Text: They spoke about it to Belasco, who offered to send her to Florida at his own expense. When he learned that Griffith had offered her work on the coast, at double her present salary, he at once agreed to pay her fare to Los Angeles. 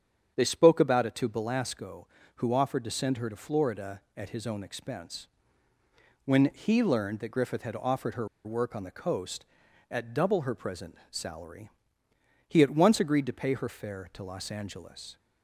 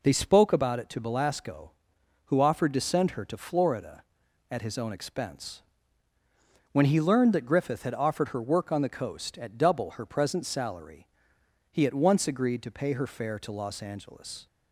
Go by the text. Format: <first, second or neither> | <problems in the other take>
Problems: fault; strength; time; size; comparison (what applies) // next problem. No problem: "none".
second | starts louder than the rest; strong; until 1.3 s; 8 dB // pauses between "her" and "work"; slight; at 8.2 s; 0.17 s long // pauses between "present" and "salary"; slight; at 10.9 s; 0.16 s long